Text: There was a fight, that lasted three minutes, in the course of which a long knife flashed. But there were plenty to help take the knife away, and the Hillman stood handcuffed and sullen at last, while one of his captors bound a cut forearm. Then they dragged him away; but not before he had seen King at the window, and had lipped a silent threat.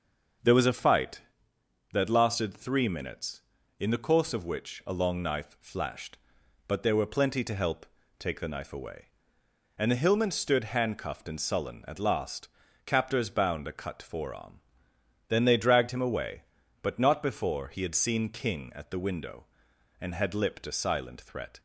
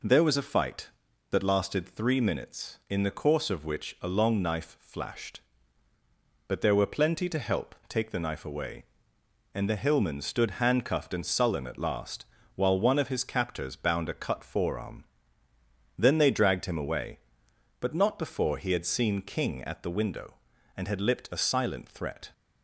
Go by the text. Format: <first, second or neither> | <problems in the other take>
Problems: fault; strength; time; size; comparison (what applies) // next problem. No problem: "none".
second | pauses between "help" and "take"; slight; at 7.8 s; 0.32 s long // skips "while one of his"; at 12.6 s